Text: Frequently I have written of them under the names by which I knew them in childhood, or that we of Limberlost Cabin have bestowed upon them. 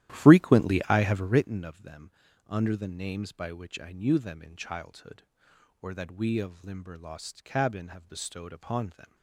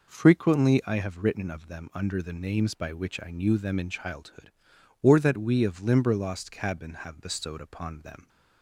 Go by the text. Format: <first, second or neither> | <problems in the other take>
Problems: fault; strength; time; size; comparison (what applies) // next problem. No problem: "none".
second | starts louder than the rest; strong; until 1.5 s; 13 dB // pauses between "them" and "under"; at 2.1 s; 0.38 s long